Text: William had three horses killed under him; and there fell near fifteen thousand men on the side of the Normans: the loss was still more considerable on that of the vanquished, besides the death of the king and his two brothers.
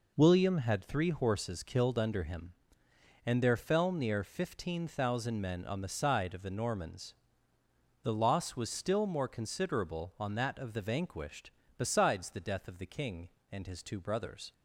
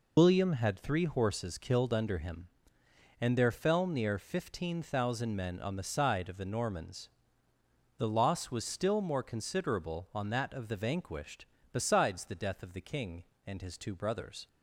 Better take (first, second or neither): first